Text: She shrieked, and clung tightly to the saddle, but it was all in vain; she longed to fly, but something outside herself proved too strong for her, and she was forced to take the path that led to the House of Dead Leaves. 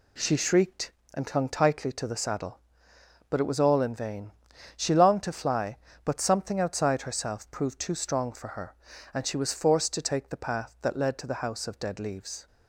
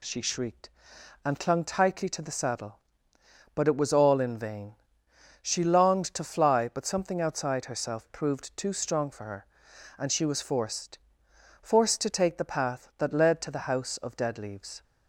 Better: first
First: none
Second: says "forced" twice; at 11.6 s

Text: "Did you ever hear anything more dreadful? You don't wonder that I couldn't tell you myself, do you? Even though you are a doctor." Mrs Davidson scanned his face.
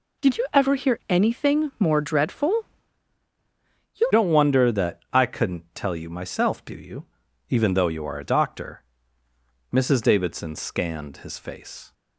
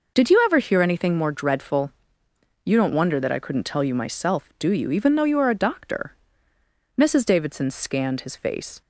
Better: second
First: changes voice at "don't"; from 4.1 s on; 7.8 s long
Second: none

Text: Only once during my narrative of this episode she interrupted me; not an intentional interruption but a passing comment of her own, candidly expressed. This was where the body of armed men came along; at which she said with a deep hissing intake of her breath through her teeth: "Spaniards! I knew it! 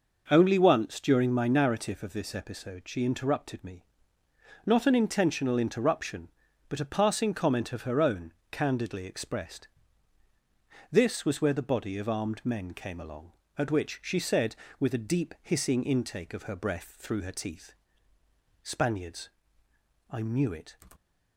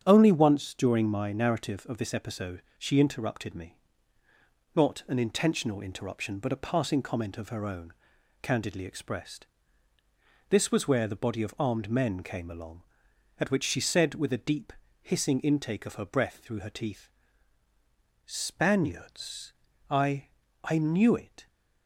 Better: first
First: none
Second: starts louder than the rest; strong; until 1.0 s; 8.5 dB // pauses between "deep" and "hissing"; slight; at 14.7 s; 0.30 s long // says "I" twice; at 20.6 s

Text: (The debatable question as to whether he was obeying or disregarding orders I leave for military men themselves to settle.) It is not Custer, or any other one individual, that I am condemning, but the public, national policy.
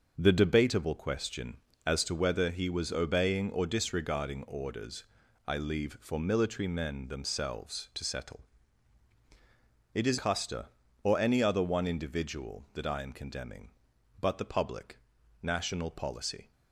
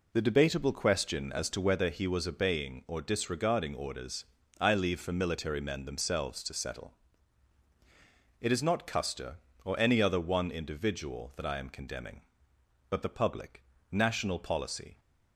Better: second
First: starts louder than the rest; until 1.1 s; 6 dB // pauses between "orders" and "I"; at 5.0 s; 0.42 s long // skips "not"; at 10.1 s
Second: pauses between "orders" and "I"; slight; at 4.2 s; 0.36 s long

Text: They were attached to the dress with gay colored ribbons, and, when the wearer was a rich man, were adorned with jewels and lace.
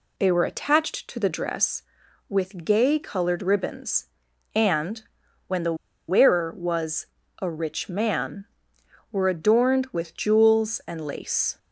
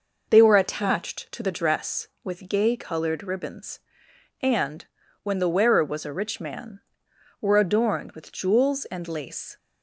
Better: second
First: pauses between "the" and "wearer"; slight; at 5.7 s; 0.34 s long // pauses between "was" and "a"; slight; at 7.0 s; 0.36 s long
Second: none

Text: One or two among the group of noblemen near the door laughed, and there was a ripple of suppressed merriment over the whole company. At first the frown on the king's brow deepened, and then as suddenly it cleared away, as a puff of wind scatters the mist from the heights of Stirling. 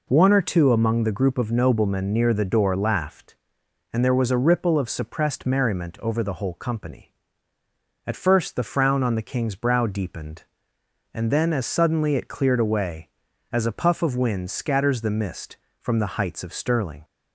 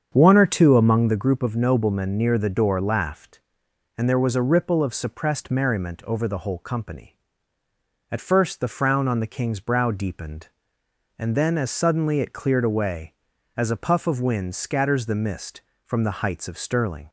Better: first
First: none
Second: starts louder than the rest; strong; until 1.3 s; 7.5 dB

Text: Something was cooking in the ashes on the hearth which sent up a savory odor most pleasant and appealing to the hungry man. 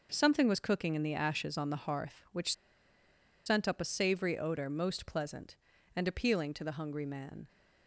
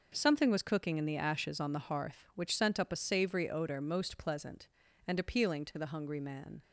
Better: second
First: pauses between "which" and "sent"; noticeable; at 2.5 s; 0.93 s long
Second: none

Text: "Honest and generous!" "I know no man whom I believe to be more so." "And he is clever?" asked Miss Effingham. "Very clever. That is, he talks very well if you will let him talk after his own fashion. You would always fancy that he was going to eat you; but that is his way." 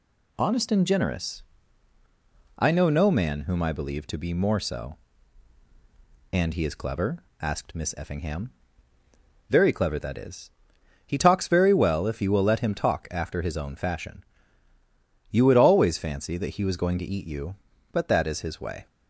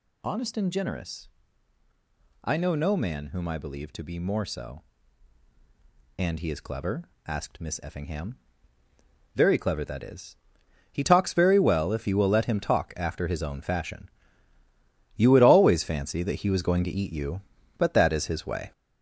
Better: first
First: none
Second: gets louder; noticeable; throughout; 5.5 dB

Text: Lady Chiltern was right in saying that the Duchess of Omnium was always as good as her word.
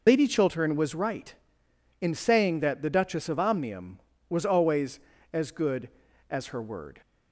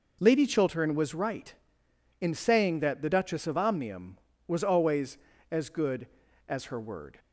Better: second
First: loses the start of "Lady"; at 0.0 s; 55 ms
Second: none

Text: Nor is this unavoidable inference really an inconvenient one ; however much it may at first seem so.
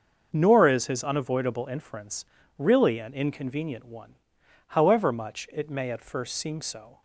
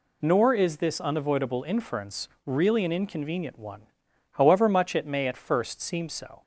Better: second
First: starts louder than the rest; until 1.3 s; 6.5 dB // says "his" for "this"; at 0.8 s // pauses between "inference" and "really"; slight; at 2.2 s; 0.32 s long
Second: pauses between "inference" and "really"; slight; at 2.2 s; 0.20 s long

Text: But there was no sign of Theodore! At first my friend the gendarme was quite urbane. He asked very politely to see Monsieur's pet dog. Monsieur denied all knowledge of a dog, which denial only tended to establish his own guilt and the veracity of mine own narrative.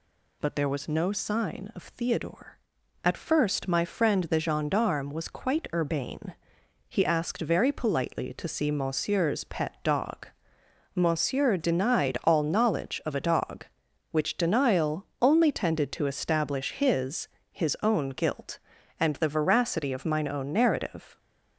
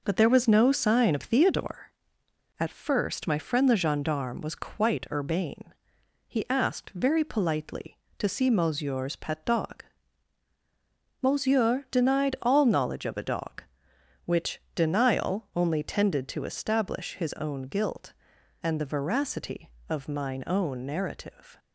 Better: second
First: pauses between "denial" and "only"; slight; at 15.0 s; 0.16 s long // says "his" twice; at 17.5 s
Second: none

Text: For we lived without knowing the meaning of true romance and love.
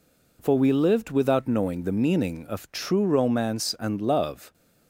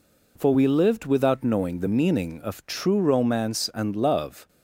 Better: neither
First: none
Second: none

